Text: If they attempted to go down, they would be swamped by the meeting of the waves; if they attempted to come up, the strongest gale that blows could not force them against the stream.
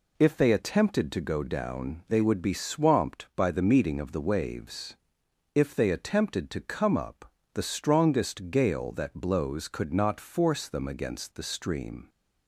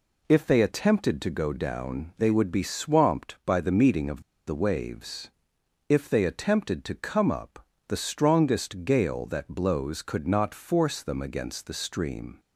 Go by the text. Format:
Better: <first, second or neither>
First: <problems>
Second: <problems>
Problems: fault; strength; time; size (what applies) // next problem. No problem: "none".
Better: first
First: none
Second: pauses between "of" and "the"; slight; at 4.2 s; 0.24 s long